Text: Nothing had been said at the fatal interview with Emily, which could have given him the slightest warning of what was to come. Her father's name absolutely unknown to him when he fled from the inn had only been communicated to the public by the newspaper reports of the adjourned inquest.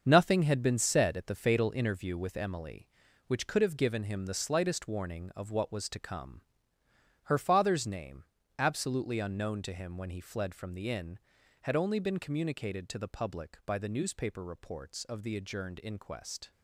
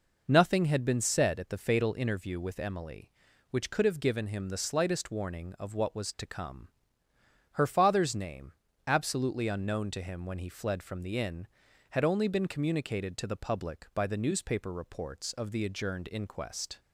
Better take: second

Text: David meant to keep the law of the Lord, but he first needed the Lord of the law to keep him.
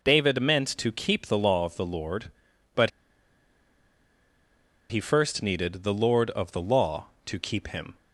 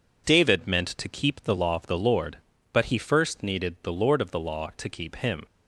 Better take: second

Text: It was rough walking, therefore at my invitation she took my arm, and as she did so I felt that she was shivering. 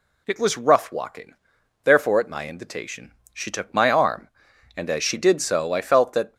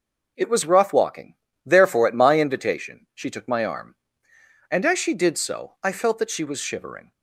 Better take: second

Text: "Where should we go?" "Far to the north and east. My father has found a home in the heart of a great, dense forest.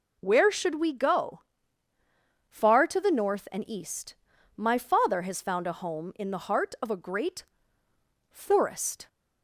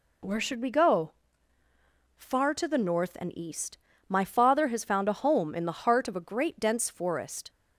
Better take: second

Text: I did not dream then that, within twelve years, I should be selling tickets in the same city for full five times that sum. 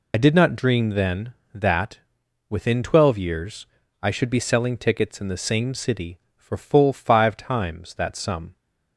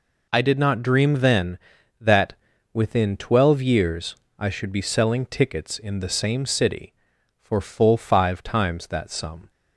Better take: second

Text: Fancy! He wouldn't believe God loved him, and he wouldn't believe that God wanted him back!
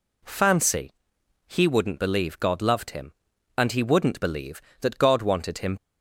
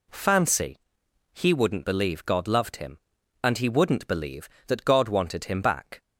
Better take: second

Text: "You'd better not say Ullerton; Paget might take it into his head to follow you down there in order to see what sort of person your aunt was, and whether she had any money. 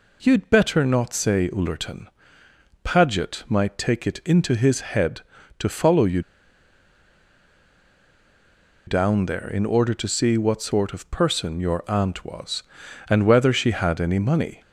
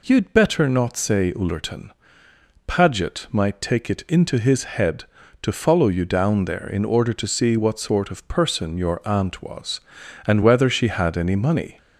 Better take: second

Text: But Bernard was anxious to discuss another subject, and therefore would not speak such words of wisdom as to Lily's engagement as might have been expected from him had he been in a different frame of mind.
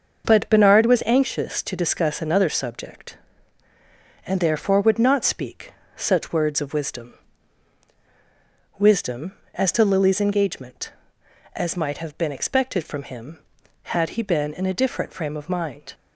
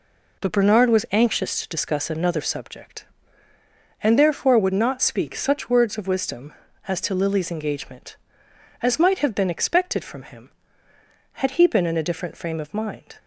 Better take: second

